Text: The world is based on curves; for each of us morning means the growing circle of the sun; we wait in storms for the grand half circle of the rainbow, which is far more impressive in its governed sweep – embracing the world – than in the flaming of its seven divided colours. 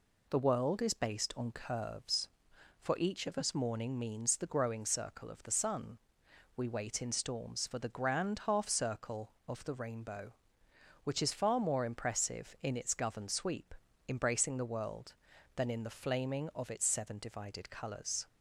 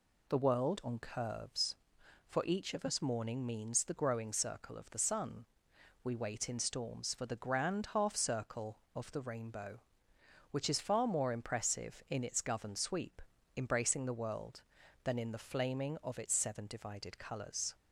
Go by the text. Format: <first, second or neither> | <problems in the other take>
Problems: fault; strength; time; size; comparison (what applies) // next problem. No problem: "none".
first | skips "is based"; at 0.8 s